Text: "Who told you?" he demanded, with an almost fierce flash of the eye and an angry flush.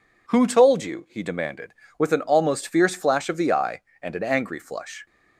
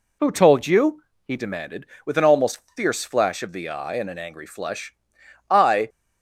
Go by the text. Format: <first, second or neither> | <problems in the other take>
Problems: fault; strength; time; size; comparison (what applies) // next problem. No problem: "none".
first | pauses between "almost" and "fierce"; slight; at 2.6 s; 0.16 s long // goes on to say "I"; slight; from 5.5 s on; 0.38 s long